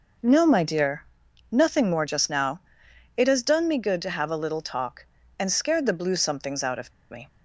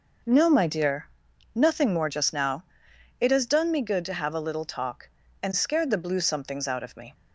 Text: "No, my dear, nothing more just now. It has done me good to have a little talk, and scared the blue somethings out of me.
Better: second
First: pauses between "of" and "me"; slight; at 6.9 s; 0.19 s long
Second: none

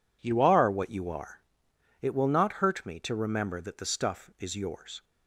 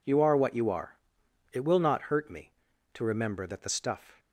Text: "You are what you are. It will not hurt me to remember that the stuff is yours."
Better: first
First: none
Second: stops before "is yours"; at 4.1 s

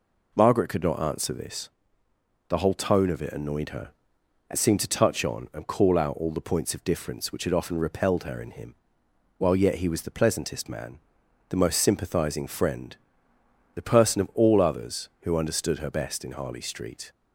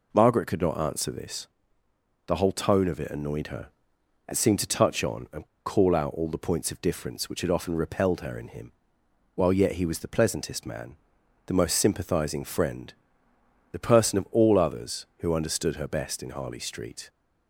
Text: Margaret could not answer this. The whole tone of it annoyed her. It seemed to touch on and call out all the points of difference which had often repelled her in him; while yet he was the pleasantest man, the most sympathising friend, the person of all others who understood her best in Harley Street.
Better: first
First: none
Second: pauses between "and" and "call"; slight; at 5.4 s; 0.21 s long

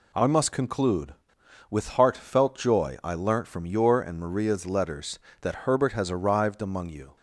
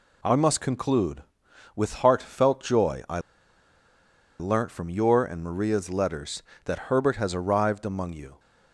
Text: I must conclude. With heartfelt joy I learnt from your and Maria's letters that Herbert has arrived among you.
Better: first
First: none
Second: pauses between "I" and "learnt"; at 3.1 s; 1.2 s long

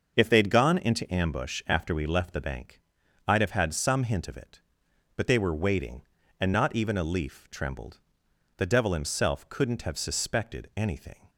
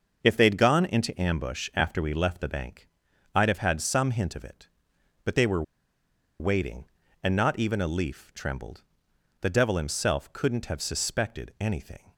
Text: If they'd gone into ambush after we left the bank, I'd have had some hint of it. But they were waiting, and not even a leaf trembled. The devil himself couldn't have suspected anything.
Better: first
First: starts louder than the rest; until 1.1 s; 6.5 dB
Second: starts louder than the rest; until 1.2 s; 6.5 dB // pauses between "were" and "waiting"; noticeable; at 5.6 s; 0.77 s long

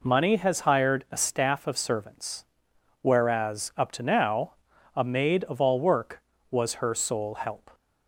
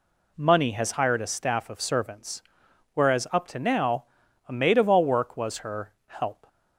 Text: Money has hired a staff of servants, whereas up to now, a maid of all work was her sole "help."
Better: first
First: none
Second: skips "sole"; at 5.9 s

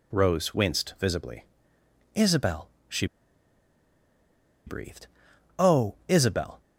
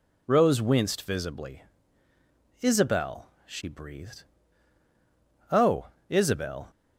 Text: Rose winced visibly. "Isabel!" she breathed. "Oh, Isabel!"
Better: second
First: pauses between "she" and "breathed"; strong; at 3.0 s; 1.6 s long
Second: none

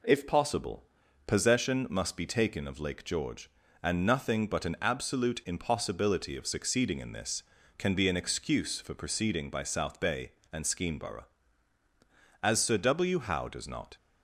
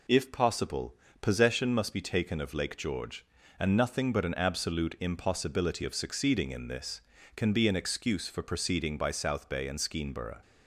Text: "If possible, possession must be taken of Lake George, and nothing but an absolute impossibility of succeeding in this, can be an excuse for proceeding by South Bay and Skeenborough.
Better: second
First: goes on to say "As Sir W Howe does not"; from 12.4 s on; 1.5 s long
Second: none

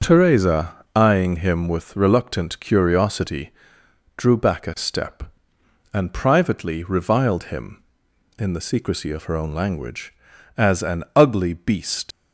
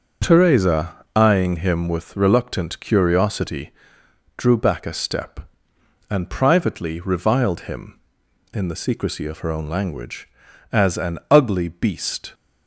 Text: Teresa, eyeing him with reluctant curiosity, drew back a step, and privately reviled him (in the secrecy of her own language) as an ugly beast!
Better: second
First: starts louder than the rest; noticeable; until 1.2 s; 6 dB // leaves "beast" unfinished; at 12.1 s; 80 ms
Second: starts louder than the rest; noticeable; until 1.4 s; 6 dB

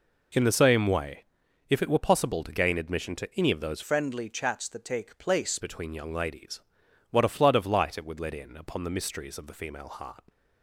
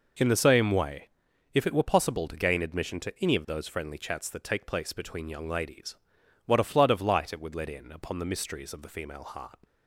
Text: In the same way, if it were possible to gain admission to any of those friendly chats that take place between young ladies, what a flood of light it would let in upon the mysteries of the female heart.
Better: second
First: changes voice from "friendly" to "place"; from 3.8 to 5.5 s; 1.7 s long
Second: none

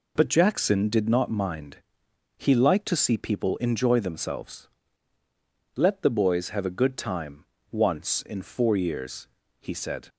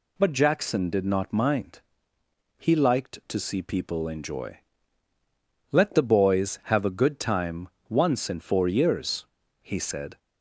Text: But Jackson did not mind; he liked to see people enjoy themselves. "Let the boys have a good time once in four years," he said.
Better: first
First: pauses between "time" and "once"; slight; at 7.4 s; 0.26 s long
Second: skips "themselves"; at 5.1 s // pauses between "time" and "once"; slight; at 7.6 s; 0.20 s long

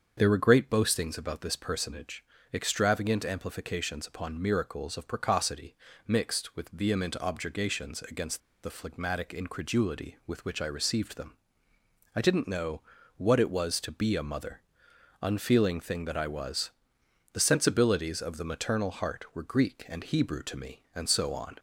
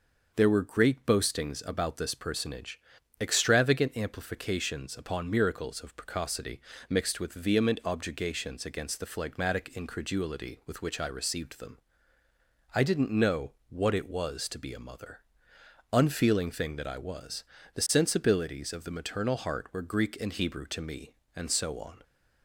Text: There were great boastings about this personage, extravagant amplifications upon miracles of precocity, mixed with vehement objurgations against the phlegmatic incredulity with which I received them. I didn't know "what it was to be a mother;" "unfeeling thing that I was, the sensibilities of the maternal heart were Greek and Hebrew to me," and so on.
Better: second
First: starts louder than the rest; until 1.1 s; 7 dB // pauses between "against" and "the"; slight; at 8.4 s; 0.22 s long // pauses between "know" and "what"; slight; at 12.8 s; 0.36 s long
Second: pauses between "know" and "what"; slight; at 13.5 s; 0.18 s long

